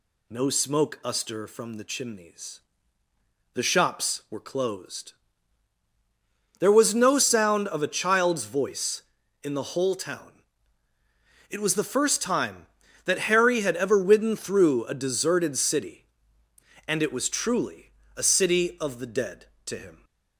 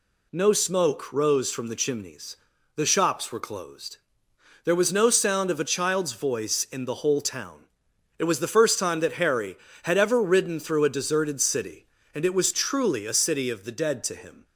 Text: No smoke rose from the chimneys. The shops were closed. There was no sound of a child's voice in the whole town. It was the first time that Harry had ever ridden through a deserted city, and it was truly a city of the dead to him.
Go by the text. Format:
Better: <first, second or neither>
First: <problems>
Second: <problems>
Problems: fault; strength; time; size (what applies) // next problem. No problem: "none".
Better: second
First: says "uster" for "rose"; at 1.0 s // pauses between "truly" and "a"; slight; at 17.8 s; 0.26 s long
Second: none